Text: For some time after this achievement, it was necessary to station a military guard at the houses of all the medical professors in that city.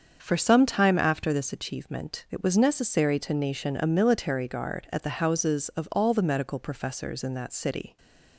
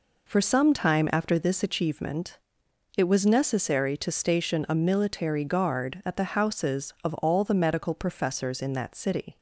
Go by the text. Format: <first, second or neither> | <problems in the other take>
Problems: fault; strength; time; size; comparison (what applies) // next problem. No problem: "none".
second | starts louder than the rest; until 1.2 s; 7 dB // says "nation" for "station"; at 3.3 s // stays silent after the last word; slight; from 7.8 s on; 0.5 s long